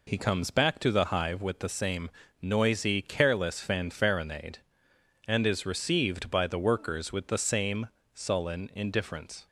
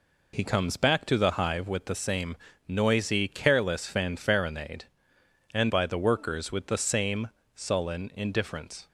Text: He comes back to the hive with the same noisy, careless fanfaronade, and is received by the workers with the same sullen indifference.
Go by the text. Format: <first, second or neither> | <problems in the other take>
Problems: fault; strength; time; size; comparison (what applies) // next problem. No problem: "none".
first | pauses between "same" and "noisy"; slight; at 2.3 s; 0.32 s long; slight in the first // skips "is received"; at 5.6 s // pauses between "same" and "sullen"; slight; at 7.2 s; 0.26 s long; slight in the first